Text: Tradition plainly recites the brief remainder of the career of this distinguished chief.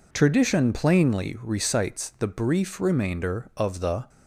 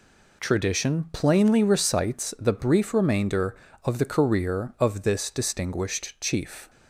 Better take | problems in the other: second | stops before "career of this distinguished chief"; at 4.0 s

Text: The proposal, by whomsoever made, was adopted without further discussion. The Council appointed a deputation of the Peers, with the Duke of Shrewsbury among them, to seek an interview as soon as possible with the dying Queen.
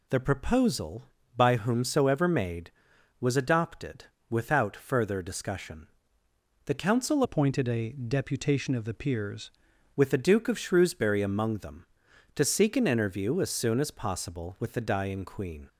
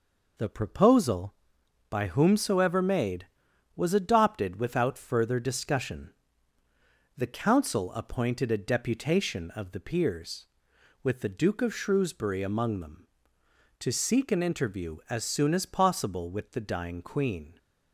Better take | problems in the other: second | pauses between "adopted" and "without"; slight; at 4.0 s; 0.24 s long // changes voice from "appointed" to "Peers"; from 7.2 to 9.5 s; 2.3 s long

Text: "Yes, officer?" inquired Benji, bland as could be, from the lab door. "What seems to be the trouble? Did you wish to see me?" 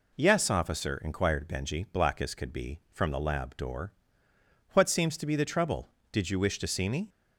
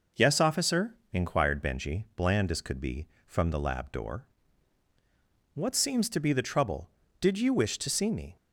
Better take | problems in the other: second | says "black" for "bland"; at 1.9 s

